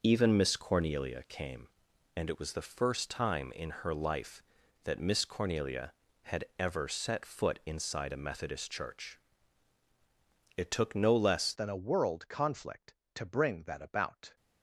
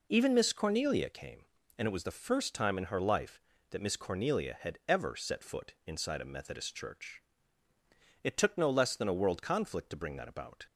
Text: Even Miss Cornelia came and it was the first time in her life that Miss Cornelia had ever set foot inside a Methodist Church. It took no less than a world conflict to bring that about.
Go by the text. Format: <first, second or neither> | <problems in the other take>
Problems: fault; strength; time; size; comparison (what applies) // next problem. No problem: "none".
second | pauses between "had" and "ever"; slight; at 6.4 s; 0.16 s long // changes voice at "than"; from 11.5 s on; 2.8 s long